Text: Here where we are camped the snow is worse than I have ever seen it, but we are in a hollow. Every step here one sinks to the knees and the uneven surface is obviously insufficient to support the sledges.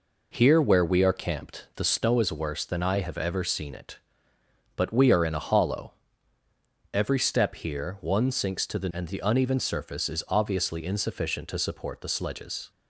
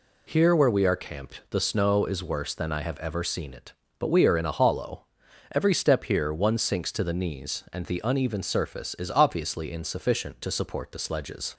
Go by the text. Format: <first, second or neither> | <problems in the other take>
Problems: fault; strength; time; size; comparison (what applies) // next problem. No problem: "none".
second | skips "knees"; at 8.8 s